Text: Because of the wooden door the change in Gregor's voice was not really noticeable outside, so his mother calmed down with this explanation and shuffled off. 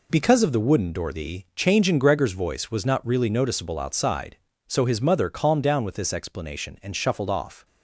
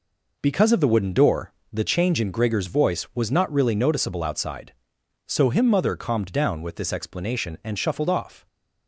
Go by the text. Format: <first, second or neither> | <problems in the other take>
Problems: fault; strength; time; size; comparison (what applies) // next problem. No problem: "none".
first | pauses between "door" and "the"; slight; at 1.5 s; 0.22 s long // says "him" for "his"; at 5.4 s